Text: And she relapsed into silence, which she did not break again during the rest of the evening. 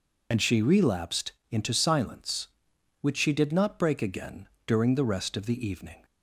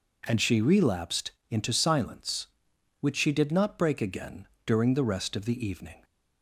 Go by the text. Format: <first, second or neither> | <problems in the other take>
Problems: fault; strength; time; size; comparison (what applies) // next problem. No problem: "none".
second | loses the start of "And"; at 0.3 s; 65 ms // pauses between "relapsed" and "into"; slight; at 1.3 s; 0.18 s long; slight in the second // pauses between "again" and "during"; slight; at 4.4 s; 0.18 s long; slight in the second